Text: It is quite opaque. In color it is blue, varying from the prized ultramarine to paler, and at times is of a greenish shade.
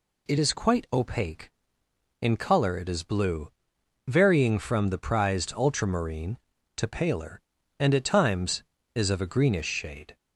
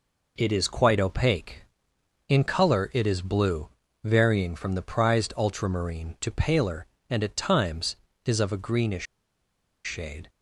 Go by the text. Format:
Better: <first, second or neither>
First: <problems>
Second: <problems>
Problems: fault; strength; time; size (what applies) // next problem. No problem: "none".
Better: first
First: none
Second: pauses between "greenish" and "shade"; noticeable; at 9.0 s; 0.79 s long